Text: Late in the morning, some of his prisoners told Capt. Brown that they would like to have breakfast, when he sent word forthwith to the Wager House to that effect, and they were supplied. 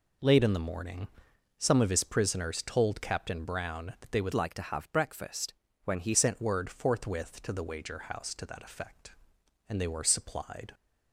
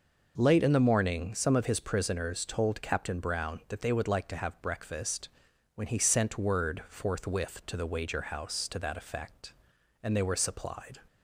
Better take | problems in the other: second | changes voice from "like" to "he"; from 4.3 to 6.1 s; 1.8 s long

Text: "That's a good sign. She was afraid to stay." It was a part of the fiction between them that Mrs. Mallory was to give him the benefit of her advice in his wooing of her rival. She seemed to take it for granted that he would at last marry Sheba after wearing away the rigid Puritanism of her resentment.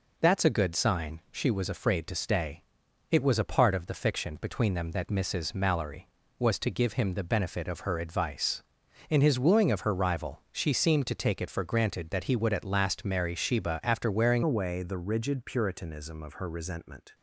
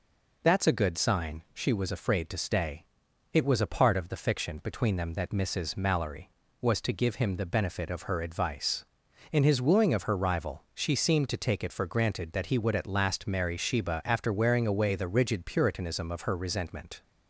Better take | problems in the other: second | changes voice at "away"; from 14.4 s on; 2.7 s long

